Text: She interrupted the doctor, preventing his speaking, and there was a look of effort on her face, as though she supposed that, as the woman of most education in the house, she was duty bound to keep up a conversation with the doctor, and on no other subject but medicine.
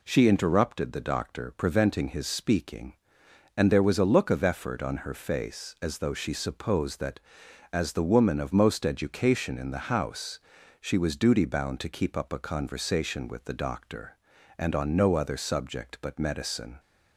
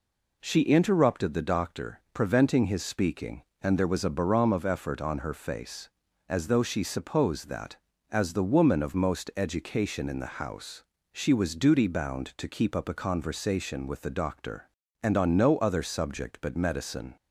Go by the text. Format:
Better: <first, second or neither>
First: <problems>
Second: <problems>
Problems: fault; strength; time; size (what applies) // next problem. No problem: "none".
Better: first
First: none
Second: says "barom" for "look"; at 4.0 s